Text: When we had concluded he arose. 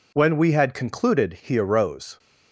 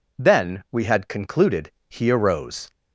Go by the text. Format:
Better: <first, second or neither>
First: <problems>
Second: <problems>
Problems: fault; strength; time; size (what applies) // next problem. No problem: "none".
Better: first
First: none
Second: says "Then" for "When"; at 0.1 s // pauses between "concluded" and "he"; slight; at 1.7 s; 0.18 s long